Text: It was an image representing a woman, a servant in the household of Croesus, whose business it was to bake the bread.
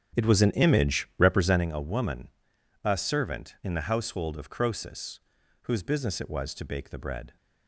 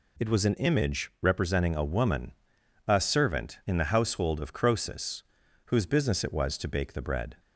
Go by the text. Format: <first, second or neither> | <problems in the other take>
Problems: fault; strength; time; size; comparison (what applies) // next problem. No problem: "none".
second | starts louder than the rest; strong; until 1.7 s; 8.5 dB